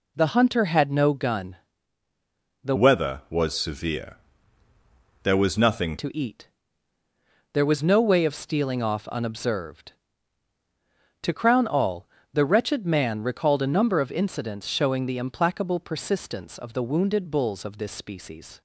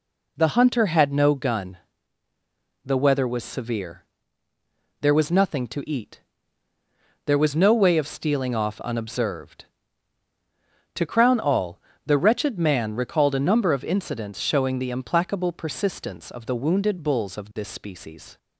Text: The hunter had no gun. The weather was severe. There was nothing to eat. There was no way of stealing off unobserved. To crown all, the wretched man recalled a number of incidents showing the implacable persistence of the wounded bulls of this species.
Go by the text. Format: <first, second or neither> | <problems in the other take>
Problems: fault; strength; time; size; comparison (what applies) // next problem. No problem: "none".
second | changes voice from "weather" to "nothing"; from 2.7 to 5.9 s; 3.2 s long